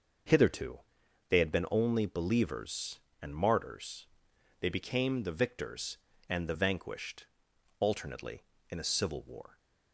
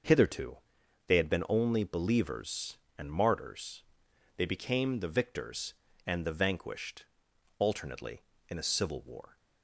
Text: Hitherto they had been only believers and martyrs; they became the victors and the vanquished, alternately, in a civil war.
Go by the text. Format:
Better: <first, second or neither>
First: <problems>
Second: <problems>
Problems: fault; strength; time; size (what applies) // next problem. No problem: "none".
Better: neither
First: starts louder than the rest; until 1.8 s; 6.5 dB // pauses between "Hitherto" and "they"; noticeable; at 0.8 s; 0.48 s long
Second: starts louder than the rest; until 1.5 s; 6.5 dB // pauses between "Hitherto" and "they"; noticeable; at 0.5 s; 0.48 s long